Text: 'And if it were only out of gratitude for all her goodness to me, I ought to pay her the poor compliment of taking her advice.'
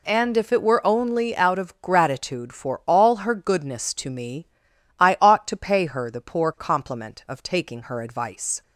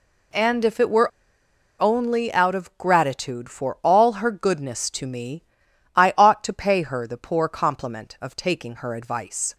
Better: first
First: none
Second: pauses between "were" and "only"; noticeable; at 1.1 s; 0.70 s long

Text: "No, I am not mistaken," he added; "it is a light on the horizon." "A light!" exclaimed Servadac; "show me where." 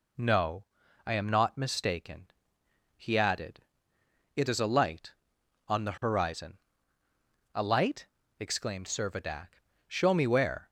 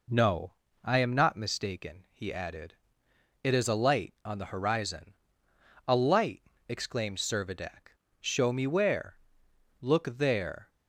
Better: first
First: none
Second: goes on to say "Look there"; noticeable; from 9.8 s on; 0.88 s long

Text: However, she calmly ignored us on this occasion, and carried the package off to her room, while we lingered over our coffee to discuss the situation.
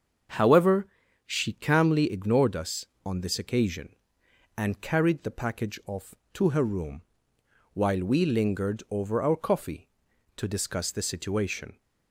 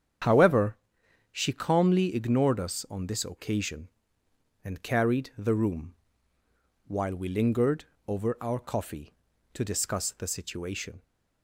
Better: first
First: starts louder than the rest; until 1.7 s; 7 dB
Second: starts louder than the rest; strong; until 1.7 s; 8.5 dB // skips "package off to her"; at 5.5 s // pauses between "lingered" and "over"; slight; at 7.8 s; 0.24 s long

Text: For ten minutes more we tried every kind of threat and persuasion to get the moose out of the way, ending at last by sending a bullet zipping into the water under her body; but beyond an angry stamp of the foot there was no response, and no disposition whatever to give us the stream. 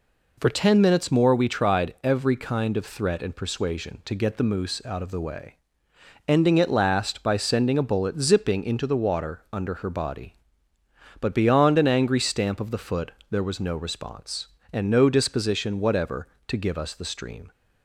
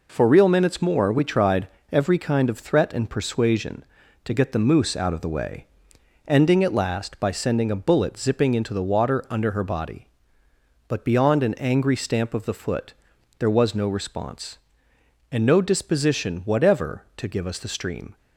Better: first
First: pauses between "foot" and "there"; slight; at 13.1 s; 0.20 s long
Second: says "real" for "ten"; at 0.2 s // pauses between "tried" and "every"; slight; at 1.6 s; 0.24 s long // pauses between "foot" and "there"; noticeable; at 12.9 s; 0.46 s long

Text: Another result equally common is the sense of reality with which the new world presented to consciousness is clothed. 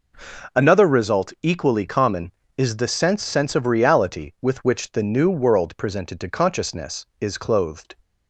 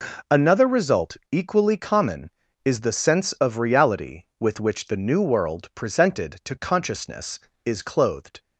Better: second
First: says "sense" twice; at 3.2 s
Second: none

